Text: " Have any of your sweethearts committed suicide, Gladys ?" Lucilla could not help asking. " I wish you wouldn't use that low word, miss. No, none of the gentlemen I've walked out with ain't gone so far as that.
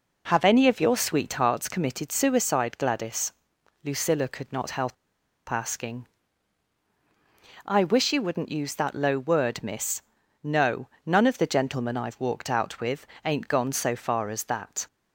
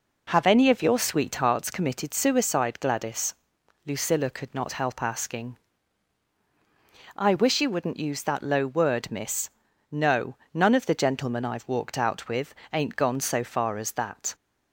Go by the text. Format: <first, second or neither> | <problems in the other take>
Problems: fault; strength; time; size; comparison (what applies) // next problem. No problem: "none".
second | starts louder than the rest; until 1.2 s; 6 dB; also in the second // pauses between "help" and "asking"; noticeable; at 4.9 s; 0.56 s long // pauses between "with" and "ain't"; slight; at 13.0 s; 0.18 s long; slight in the second